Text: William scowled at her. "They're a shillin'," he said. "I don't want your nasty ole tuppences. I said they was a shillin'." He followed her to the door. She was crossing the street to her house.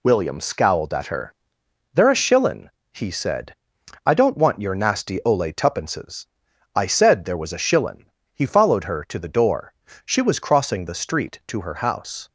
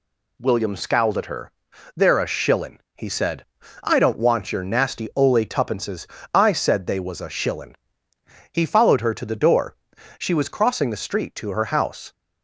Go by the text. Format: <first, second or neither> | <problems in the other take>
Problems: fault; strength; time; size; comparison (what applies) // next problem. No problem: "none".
second | says "there" for "they"; at 7.2 s